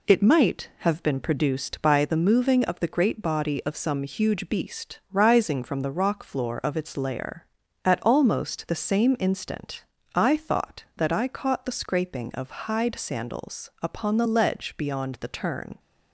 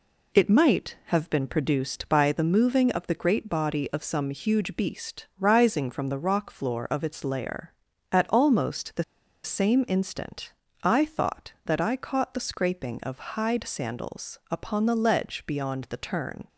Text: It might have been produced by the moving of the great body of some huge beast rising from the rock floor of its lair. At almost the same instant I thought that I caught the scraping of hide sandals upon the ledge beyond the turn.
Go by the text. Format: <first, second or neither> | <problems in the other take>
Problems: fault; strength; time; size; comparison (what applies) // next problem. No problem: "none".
first | pauses between "the" and "same"; at 9.0 s; 0.40 s long // pauses between "instant" and "I"; slight; at 10.5 s; 0.30 s long; slight in the first